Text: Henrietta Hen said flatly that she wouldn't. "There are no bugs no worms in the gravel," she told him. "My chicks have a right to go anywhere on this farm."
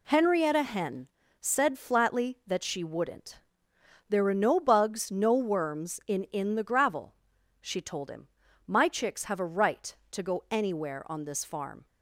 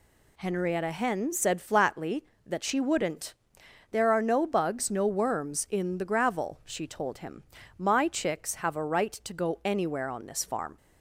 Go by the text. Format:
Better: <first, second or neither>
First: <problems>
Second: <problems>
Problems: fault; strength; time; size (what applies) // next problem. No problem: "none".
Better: second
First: pauses between "Hen" and "said"; slight; at 1.0 s; 0.32 s long // says "in" twice; at 6.2 s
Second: none